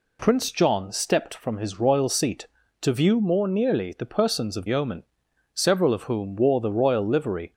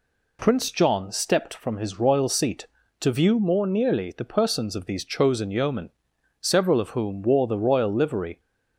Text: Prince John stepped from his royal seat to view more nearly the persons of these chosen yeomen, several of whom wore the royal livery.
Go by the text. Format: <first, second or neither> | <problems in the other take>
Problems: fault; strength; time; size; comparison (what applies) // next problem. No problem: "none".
second | skips "these chosen"; at 4.6 s